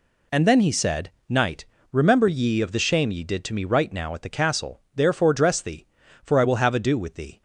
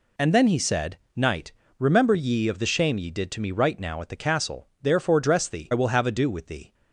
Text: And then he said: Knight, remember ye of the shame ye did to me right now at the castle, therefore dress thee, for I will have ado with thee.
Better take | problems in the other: first | skips "for"; at 5.7 s

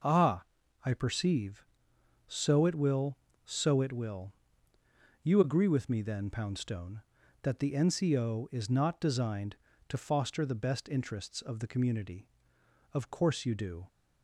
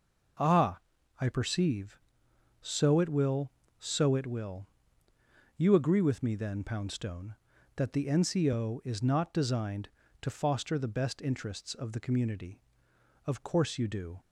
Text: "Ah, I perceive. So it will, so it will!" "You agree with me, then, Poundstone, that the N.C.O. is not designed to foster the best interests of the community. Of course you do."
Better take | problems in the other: neither | none

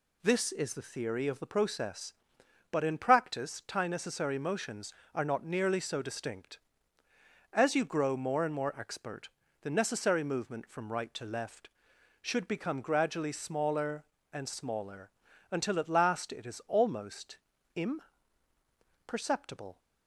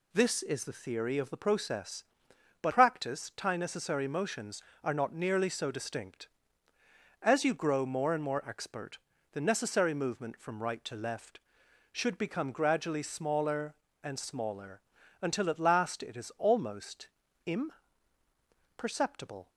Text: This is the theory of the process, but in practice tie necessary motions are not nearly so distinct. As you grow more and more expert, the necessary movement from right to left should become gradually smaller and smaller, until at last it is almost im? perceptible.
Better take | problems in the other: first | skips "in"; at 2.7 s // pauses between "almost" and "im"; at 17.0 s; 0.40 s long; also in the first

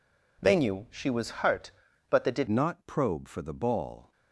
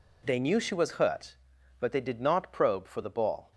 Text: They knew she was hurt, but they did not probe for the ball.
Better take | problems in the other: second | changes voice at "not"; from 2.4 s on; 1.7 s long

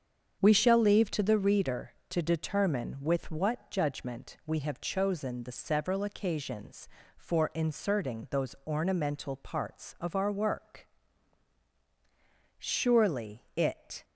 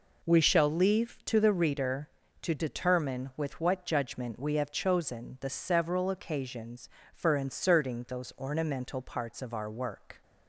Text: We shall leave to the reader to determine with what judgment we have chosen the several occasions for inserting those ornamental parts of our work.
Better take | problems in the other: second | starts louder than the rest; strong; until 1.4 s; 7.5 dB // goes on to say "Surely it"; from 12.5 s on; 1.4 s long

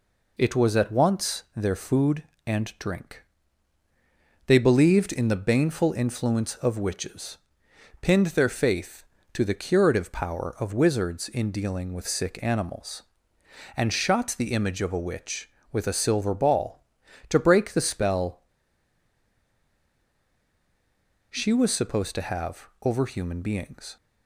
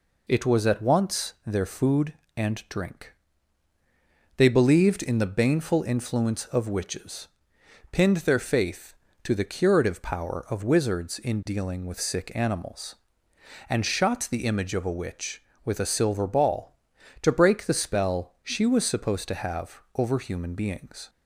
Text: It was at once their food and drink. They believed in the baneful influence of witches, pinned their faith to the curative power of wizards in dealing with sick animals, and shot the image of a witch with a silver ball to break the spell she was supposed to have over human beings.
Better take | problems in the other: second | pauses between "spell" and "she"; strong; at 18.4 s; 2.8 s long

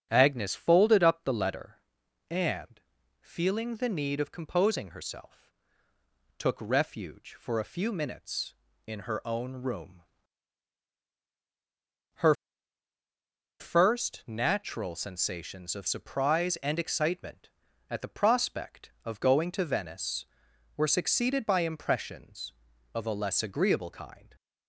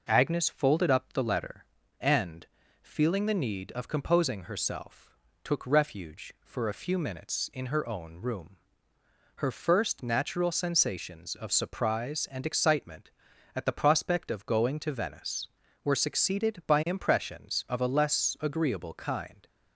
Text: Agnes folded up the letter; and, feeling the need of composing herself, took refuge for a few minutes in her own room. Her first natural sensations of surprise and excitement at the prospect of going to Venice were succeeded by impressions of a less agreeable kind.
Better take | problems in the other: second | starts louder than the rest; strong; until 1.1 s; 8 dB // pauses between "Her" and "first"; strong; at 12.3 s; 1.2 s long

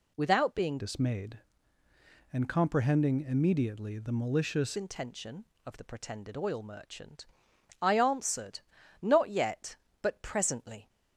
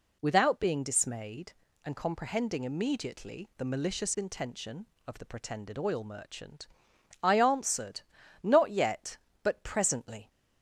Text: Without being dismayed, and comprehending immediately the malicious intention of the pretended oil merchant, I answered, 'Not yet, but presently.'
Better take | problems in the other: second | changes voice from "dismayed" to "malicious"; from 0.7 to 4.7 s; 4.0 s long

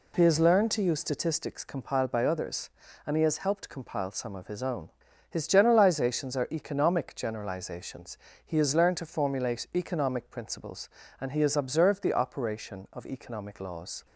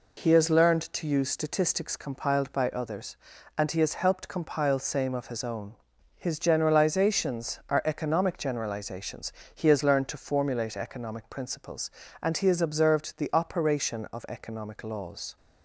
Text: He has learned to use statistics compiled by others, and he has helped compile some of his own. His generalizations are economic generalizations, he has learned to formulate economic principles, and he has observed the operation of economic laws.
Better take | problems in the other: first | says "same" for "some"; at 4.8 s

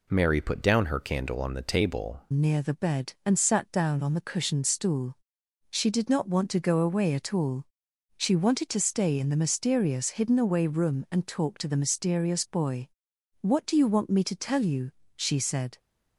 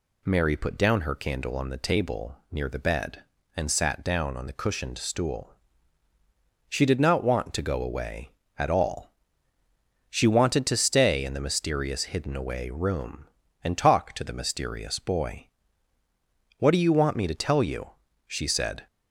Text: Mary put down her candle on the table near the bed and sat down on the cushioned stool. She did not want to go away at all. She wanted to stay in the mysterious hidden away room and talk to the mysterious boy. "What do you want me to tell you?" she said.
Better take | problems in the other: second | changes voice at "near"; from 2.3 s on; 13.4 s long

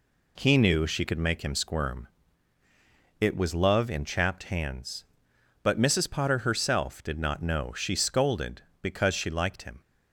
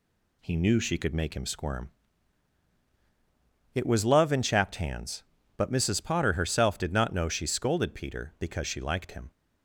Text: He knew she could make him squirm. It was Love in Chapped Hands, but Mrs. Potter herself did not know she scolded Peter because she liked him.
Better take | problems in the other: second | skips "Peter"; at 8.7 s

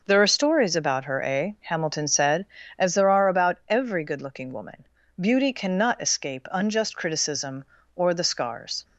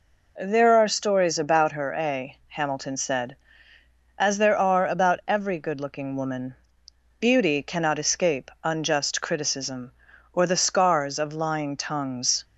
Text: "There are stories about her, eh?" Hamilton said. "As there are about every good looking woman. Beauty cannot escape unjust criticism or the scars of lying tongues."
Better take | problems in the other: second | stops before "of lying tongues"; at 8.8 s

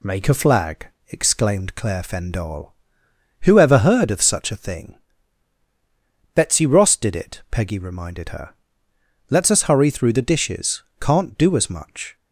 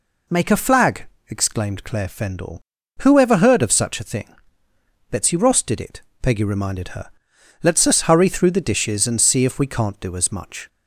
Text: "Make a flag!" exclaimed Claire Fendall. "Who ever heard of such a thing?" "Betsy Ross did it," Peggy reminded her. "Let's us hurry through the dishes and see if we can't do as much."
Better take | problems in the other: second | skips "and see if we"; at 10.9 s

